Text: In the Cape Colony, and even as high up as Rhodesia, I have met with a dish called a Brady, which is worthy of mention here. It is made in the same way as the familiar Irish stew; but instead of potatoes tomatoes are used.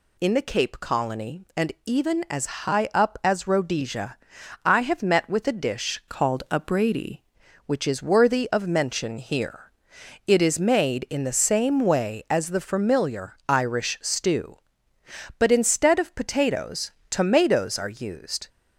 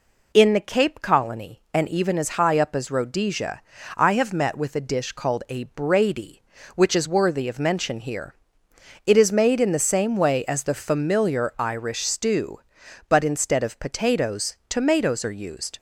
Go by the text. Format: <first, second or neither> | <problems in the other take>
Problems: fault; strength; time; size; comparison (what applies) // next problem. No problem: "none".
second | pauses between "as" and "high"; slight; at 2.4 s; 0.18 s long // changes voice from "called" to "Brady"; from 6.0 to 7.1 s; 1.1 s long // pauses between "potatoes" and "tomatoes"; slight; at 16.9 s; 0.18 s long